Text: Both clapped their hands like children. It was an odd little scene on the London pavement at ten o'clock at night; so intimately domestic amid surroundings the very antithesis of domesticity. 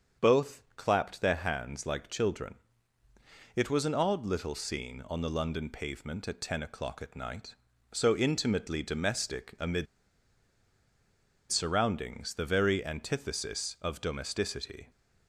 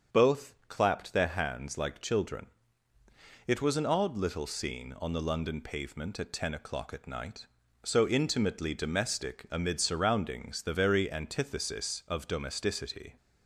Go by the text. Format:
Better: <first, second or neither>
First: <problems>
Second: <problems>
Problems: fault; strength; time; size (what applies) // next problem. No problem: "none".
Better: second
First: starts louder than the rest; strong; until 1.3 s; 7 dB // pauses between "amid" and "surroundings"; strong; at 9.8 s; 1.6 s long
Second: starts louder than the rest; strong; until 1.2 s; 7 dB